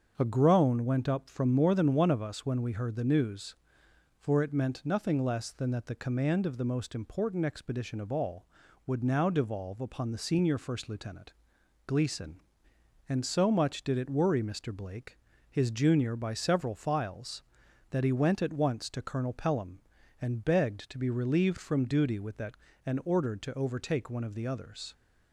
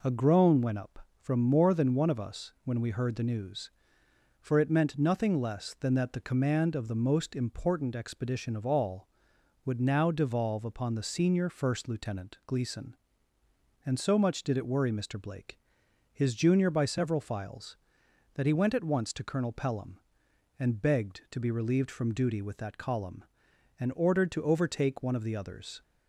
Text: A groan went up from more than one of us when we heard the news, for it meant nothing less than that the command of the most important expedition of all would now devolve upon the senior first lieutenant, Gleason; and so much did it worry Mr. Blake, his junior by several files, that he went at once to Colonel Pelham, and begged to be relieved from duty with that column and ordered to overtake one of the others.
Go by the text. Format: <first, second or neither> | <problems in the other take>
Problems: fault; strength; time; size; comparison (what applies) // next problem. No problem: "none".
second | starts louder than the rest; until 1.1 s; 7 dB // skips "column"; at 22.7 s